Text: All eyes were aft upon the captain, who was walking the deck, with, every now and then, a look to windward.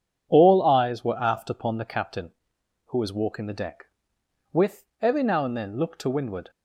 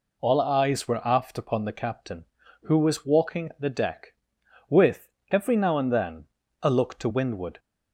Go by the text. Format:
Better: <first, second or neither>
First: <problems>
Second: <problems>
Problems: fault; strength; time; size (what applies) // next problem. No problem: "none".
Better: second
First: skips "a"; at 5.7 s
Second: none